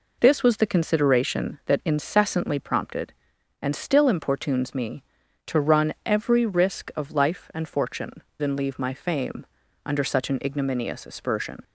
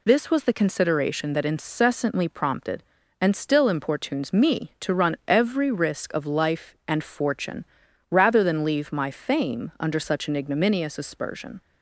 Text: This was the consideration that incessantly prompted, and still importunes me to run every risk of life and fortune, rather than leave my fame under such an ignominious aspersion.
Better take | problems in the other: second | skips "rather"; at 8.3 s // pauses between "fame" and "under"; at 9.4 s; 0.40 s long

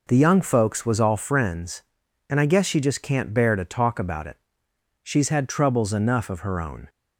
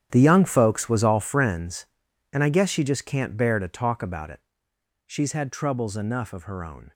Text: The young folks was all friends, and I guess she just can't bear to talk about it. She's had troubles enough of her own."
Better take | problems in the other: first | gets quieter; strong; throughout; 15 dB

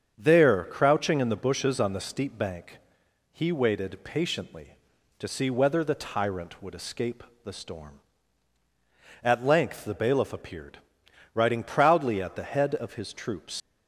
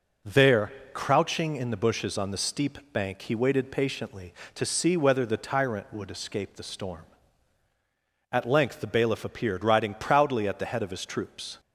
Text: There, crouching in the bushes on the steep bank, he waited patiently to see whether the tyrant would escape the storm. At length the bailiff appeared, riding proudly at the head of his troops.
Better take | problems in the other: second | starts louder than the rest; strong; until 1.1 s; 7.5 dB // pauses between "escape" and "the"; slight; at 7.2 s; 0.18 s long // leaves "troops" unfinished; at 13.6 s; 105 ms

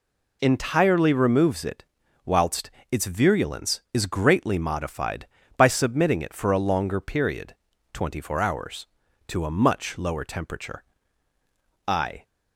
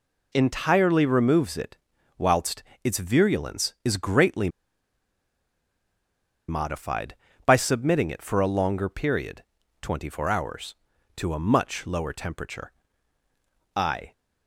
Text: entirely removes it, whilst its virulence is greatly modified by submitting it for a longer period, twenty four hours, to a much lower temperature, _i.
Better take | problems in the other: first | pauses between "whilst" and "its"; slight; at 2.6 s; 0.20 s long; slight in the first // pauses between "greatly" and "modified"; strong; at 4.4 s; 1.9 s long

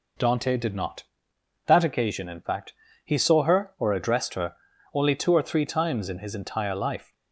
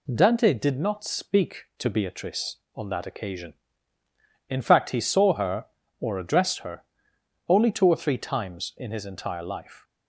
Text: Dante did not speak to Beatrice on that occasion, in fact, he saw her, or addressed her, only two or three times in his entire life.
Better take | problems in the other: second | skips "speak to Beatrice on"; at 1.3 s

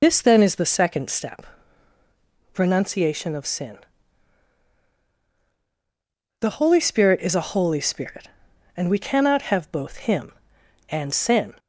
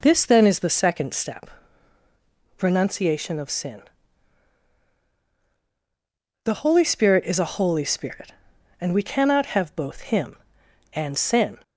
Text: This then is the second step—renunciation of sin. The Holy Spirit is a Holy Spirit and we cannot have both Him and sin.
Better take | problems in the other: second | loses the start of "This"; at 0.0 s; 60 ms

